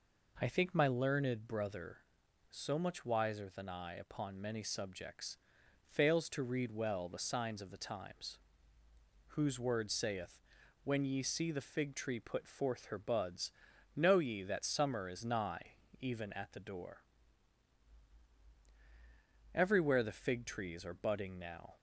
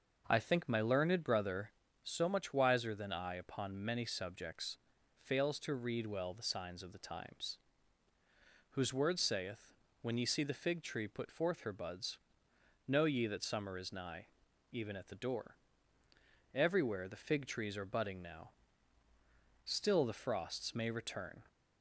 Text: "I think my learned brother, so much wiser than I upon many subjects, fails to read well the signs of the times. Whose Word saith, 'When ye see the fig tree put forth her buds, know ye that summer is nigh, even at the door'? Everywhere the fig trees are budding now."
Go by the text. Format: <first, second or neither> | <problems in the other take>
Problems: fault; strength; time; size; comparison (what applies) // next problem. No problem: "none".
first | starts louder than the rest; noticeable; until 1.2 s; 6 dB // goes on to say "Still the frosts may return"; strong; from 19.6 s on; 1.8 s long